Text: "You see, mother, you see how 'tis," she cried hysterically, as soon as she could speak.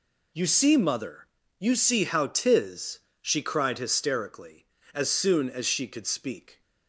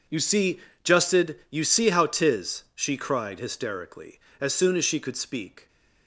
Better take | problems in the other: first | says "justed" for "mother"; at 0.8 s

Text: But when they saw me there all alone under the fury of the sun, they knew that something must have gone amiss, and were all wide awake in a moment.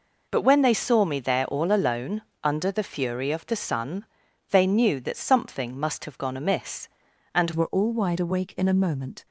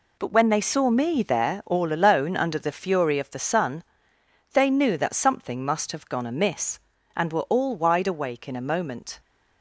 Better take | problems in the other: second | pauses between "alone" and "under"; slight; at 2.2 s; 0.22 s long // changes voice at "were"; from 7.5 s on; 1.7 s long

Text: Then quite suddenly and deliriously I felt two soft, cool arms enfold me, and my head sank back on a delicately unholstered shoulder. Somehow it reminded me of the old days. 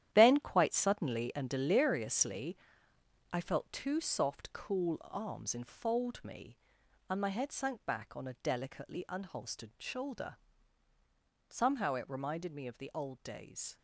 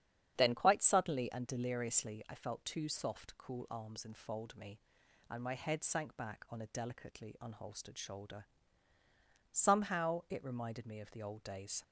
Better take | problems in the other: second | gets quieter; strong; throughout; 10 dB // starts louder than the rest; strong; until 1.1 s; 11 dB; strong in the second // pauses between "deliriously" and "I"; noticeable; at 2.5 s; 0.74 s long

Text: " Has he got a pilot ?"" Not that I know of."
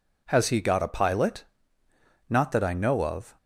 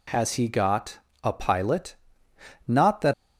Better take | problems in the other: first | pauses between "got" and "a"; slight; at 1.0 s; 0.22 s long // stops before "I know of"; at 3.1 s

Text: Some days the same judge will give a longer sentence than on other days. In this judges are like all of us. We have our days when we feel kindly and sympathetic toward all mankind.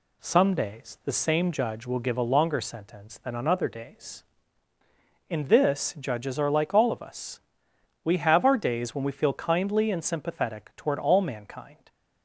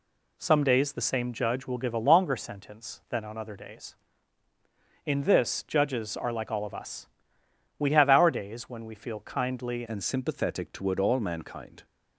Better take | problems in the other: first | changes voice at "and"; from 9.8 s on; 2.0 s long

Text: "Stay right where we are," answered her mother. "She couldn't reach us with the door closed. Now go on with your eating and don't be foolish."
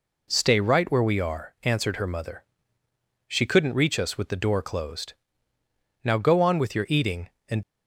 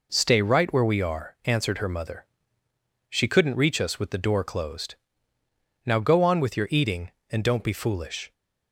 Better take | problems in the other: second | stops before "don't be foolish"; at 7.6 s

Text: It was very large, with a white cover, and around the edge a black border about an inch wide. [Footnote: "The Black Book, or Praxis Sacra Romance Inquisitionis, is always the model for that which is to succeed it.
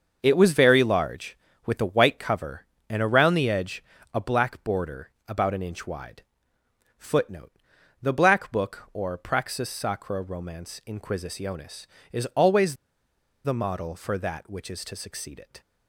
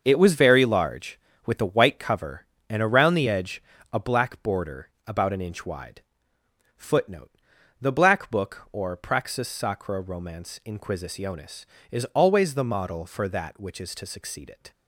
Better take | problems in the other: second | starts louder than the rest; until 1.2 s; 6.5 dB; also in the second // pauses between "edge" and "a"; slight; at 3.8 s; 0.32 s long; slight in the second // pauses between "border" and "about"; slight; at 5.0 s; 0.18 s long; slight in the second // pauses between "always" and "the"; noticeable; at 12.7 s; 0.68 s long

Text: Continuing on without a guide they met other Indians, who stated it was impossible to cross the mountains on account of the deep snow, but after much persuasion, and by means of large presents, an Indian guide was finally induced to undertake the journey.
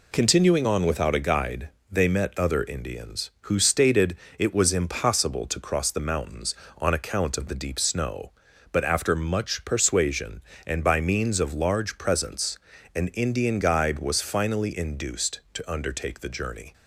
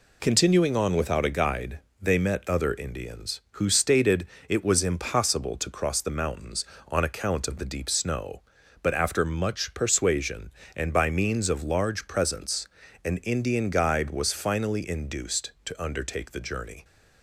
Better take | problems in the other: neither | pauses between "guide" and "they"; slight; the same in both // pauses between "stated" and "it"; slight; the same in both

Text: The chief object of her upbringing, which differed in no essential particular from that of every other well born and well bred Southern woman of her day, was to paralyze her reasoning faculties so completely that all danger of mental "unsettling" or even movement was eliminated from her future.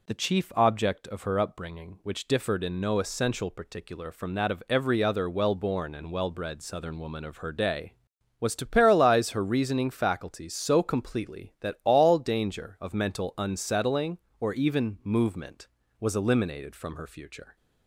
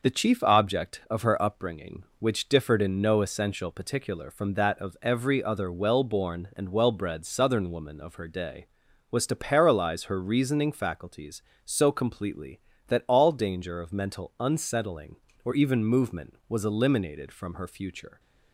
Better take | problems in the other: neither | none

